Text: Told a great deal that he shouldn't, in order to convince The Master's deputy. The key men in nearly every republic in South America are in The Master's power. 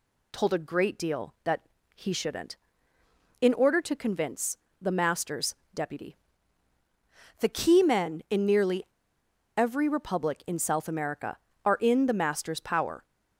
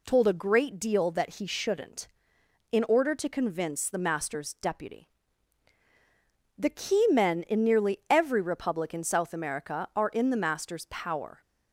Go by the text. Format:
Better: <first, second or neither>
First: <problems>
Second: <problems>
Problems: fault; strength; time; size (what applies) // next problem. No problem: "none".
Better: second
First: pauses between "that" and "he"; slight; at 1.6 s; 0.34 s long // pauses between "convince" and "The"; slight; at 4.5 s; 0.24 s long // pauses between "Master's" and "deputy"; slight; at 5.5 s; 0.20 s long // pauses between "nearly" and "every"; noticeable; at 8.8 s; 0.72 s long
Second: none